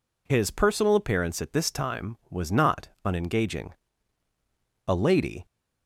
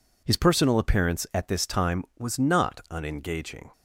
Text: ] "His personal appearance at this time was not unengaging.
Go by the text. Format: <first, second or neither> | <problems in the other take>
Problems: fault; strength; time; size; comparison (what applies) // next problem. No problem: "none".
second | pauses between "not" and "unengaging"; slight; at 2.8 s; 0.18 s long // goes on to say "A lady"; from 4.8 s on; 0.58 s long